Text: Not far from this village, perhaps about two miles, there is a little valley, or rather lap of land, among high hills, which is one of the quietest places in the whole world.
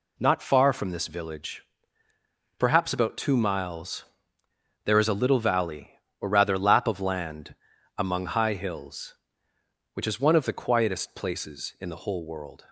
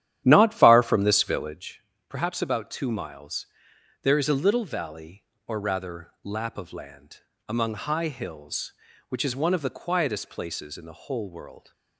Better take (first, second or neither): first